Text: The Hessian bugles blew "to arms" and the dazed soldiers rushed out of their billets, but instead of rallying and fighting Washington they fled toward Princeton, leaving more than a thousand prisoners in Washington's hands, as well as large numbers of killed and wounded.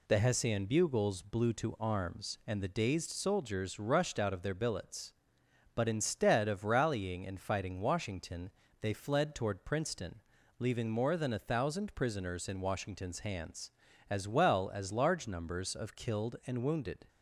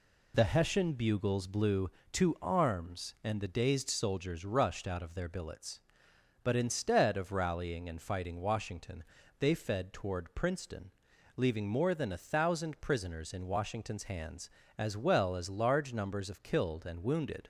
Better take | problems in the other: first | pauses between "Washington" and "they"; slight; at 9.0 s; 0.34 s long; slight in the first // says "fed" for "fled"; at 9.5 s

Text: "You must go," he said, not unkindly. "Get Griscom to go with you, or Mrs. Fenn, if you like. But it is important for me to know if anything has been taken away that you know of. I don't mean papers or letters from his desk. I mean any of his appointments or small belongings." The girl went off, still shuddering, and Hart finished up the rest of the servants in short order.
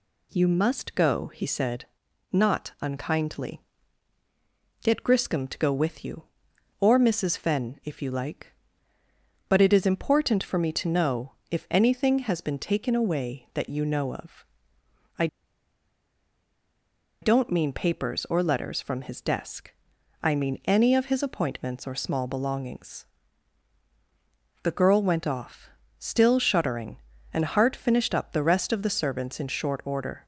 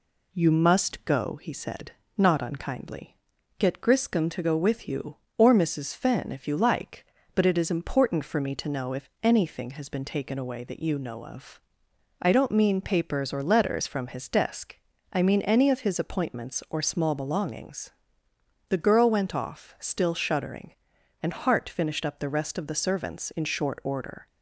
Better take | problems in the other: second | pauses between "know" and "if"; slight; at 11.3 s; 0.18 s long // pauses between "I" and "don't"; strong; at 15.2 s; 1.9 s long

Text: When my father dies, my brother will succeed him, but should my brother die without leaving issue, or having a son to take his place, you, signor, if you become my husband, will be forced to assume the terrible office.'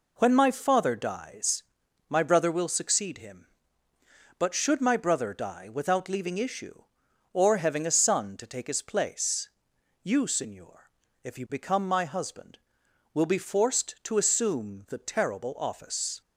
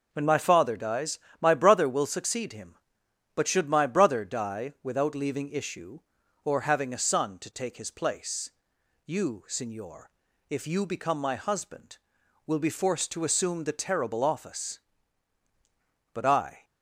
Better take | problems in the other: first | goes on to say "But I"; from 16.1 s on; 0.52 s long

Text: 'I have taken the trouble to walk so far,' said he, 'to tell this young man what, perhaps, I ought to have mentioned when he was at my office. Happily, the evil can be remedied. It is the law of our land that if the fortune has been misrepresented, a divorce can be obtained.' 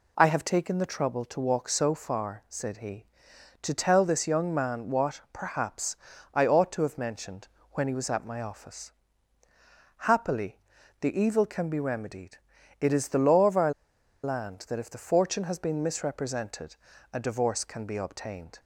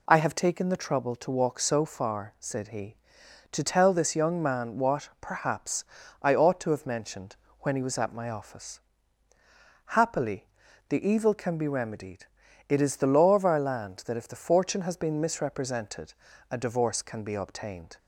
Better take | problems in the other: second | pauses between "mentioned" and "when"; slight; at 7.4 s; 0.24 s long; slight in the second // pauses between "our" and "land"; noticeable; at 13.7 s; 0.52 s long

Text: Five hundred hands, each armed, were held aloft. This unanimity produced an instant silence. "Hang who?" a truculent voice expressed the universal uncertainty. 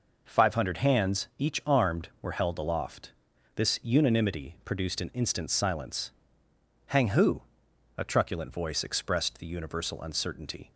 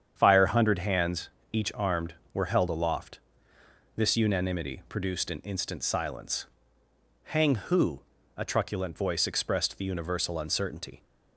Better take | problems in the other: first | starts louder than the rest; strong; until 1.1 s; 8 dB // says "Fire" for "Five"; at 0.1 s

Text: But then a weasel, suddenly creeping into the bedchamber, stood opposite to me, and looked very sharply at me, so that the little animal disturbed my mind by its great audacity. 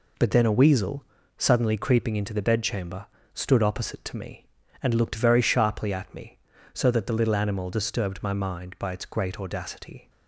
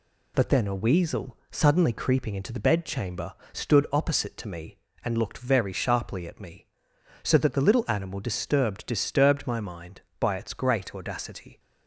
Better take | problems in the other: first | says "disturbed" twice; at 8.8 s

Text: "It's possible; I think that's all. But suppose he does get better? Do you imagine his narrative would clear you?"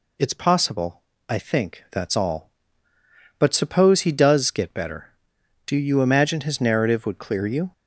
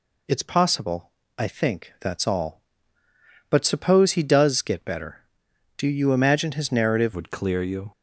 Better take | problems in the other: first | changes voice at "would"; from 7.1 s on; 0.8 s long

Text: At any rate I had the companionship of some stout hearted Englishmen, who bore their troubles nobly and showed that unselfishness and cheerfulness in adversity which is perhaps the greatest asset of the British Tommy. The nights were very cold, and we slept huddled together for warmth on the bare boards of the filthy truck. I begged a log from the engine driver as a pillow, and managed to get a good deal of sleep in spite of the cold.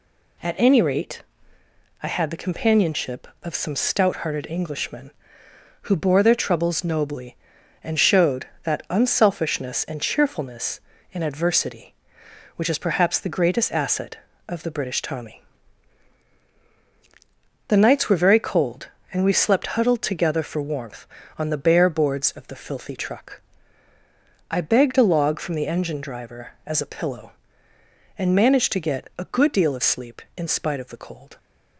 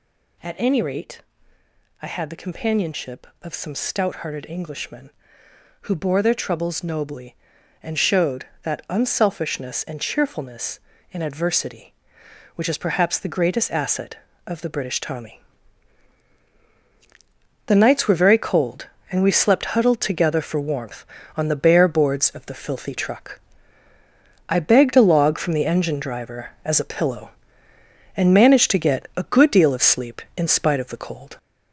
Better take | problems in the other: first | gets louder; noticeable; throughout; 5 dB // pauses between "rate" and "I"; noticeable; at 1.2 s; 0.78 s long; noticeable in the first

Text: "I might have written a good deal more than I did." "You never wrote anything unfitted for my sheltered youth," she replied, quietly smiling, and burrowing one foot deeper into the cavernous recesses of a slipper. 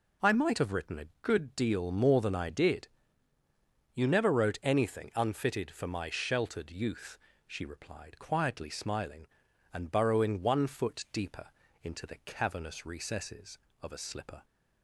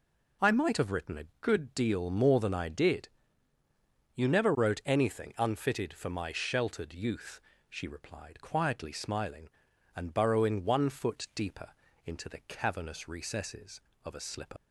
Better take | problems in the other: first | pauses between "deeper" and "into"; slight; at 11.7 s; 0.32 s long; slight in the first // leaves "slipper" unfinished; at 14.5 s; 100 ms

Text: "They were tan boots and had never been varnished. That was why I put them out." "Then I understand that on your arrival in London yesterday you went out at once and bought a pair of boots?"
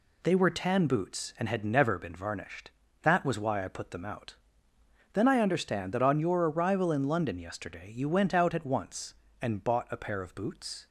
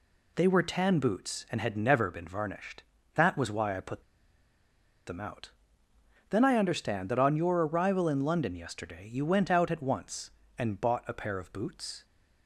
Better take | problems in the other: first | pauses between "put" and "them"; at 4.0 s; 1.0 s long

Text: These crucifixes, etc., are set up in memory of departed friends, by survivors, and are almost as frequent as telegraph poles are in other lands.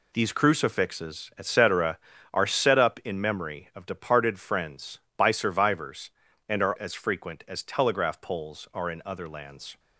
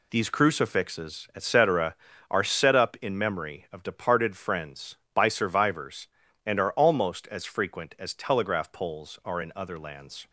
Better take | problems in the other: second | skips "almost"; at 6.7 s

